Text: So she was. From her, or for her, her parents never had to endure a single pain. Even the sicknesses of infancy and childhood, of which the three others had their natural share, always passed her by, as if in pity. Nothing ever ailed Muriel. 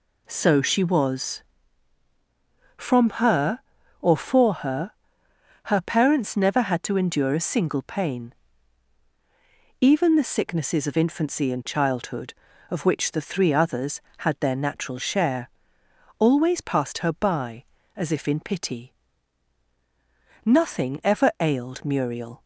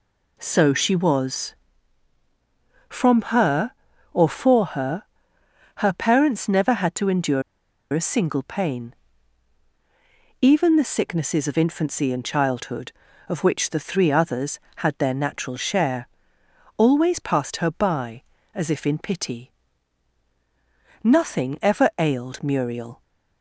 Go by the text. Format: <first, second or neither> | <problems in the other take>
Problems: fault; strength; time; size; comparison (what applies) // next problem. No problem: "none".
first | pauses between "endure" and "a"; noticeable; at 7.4 s; 0.51 s long